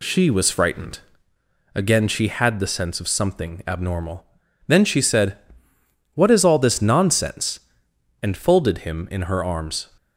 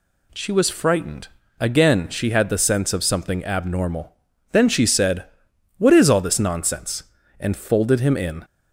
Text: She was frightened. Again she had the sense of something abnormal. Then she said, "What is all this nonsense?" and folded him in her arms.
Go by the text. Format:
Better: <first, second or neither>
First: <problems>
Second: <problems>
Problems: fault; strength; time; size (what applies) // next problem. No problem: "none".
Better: first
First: none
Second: stops before "her arms"; at 8.4 s